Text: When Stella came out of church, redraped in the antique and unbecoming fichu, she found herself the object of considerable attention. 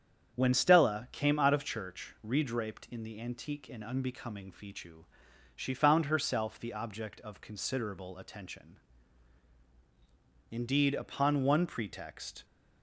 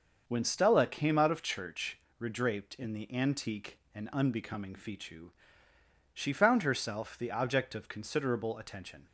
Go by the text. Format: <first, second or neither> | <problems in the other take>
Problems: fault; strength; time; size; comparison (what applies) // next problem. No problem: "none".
second | starts louder than the rest; strong; until 1.3 s; 8 dB; noticeable in the second // goes on to say "Indeed upon one pretext"; strong; from 10.5 s on; 1.9 s long